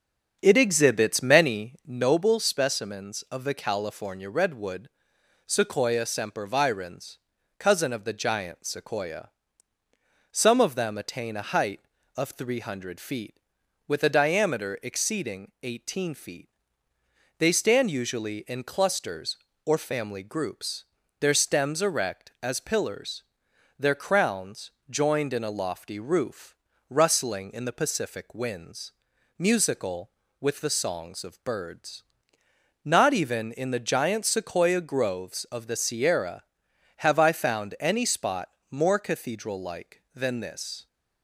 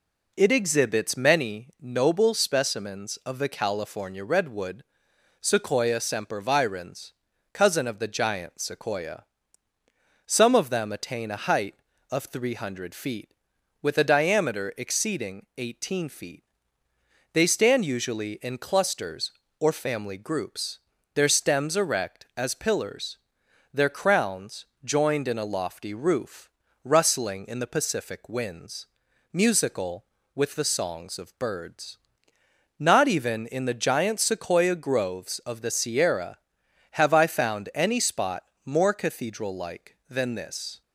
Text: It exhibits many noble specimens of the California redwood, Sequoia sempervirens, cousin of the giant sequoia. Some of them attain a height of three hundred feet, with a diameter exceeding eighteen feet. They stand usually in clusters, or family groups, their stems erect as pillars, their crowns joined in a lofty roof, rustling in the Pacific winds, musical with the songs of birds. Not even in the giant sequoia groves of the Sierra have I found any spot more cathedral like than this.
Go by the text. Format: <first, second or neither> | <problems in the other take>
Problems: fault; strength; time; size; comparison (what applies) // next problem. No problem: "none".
second | starts louder than the rest; strong; until 2.2 s; 8 dB // pauses between "crowns" and "joined"; slight; at 24.7 s; 0.18 s long; slight in the second // pauses between "spot" and "more"; slight; at 38.4 s; 0.22 s long; slight in the second